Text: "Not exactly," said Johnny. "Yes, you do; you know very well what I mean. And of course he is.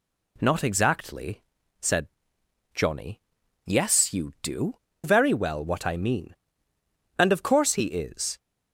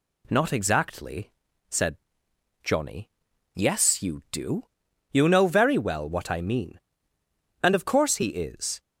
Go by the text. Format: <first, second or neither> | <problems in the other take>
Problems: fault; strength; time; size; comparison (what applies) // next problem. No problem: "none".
second | pauses between "said" and "Johnny"; noticeable; at 2.0 s; 0.66 s long; noticeable in the second // skips "you know"; at 4.9 s